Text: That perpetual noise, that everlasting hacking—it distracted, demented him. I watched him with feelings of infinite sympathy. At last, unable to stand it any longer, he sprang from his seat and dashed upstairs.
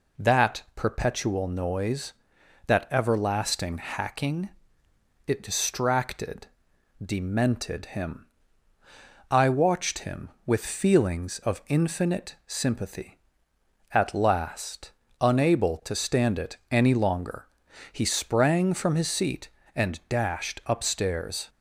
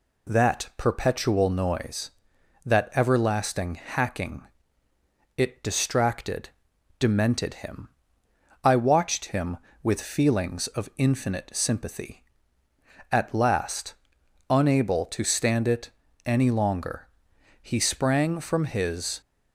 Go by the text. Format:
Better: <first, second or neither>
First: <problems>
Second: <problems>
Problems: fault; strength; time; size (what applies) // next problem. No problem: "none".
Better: first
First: none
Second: pauses between "it" and "any"; slight; at 15.9 s; 0.34 s long // stops before "seat and dashed upstairs"; at 19.2 s